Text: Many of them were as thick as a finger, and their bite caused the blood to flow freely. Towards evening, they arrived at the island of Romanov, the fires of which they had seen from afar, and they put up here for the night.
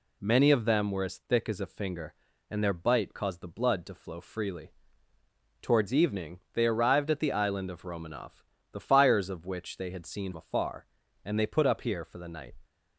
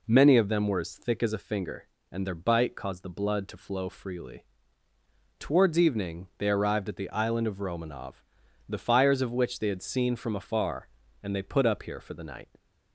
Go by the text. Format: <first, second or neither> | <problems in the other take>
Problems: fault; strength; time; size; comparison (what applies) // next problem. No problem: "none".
second | skips "from"; at 10.3 s